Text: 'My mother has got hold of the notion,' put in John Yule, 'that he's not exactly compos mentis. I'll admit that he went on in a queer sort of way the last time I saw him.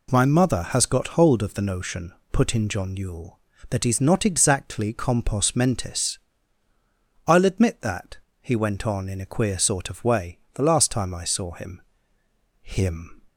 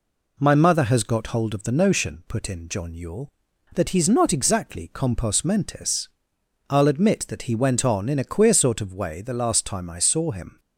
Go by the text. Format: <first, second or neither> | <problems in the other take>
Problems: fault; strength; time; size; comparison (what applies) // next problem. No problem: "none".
second | pauses between "that" and "he"; slight; at 8.1 s; 0.24 s long // pauses between "way" and "the"; slight; at 10.3 s; 0.16 s long // says "him" twice; at 12.6 s